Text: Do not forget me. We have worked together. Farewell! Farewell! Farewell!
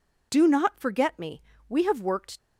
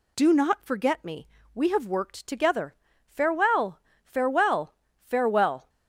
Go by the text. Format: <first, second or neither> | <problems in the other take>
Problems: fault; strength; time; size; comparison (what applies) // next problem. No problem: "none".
second | stops before "together Farewell Farewell Farewell"; at 2.3 s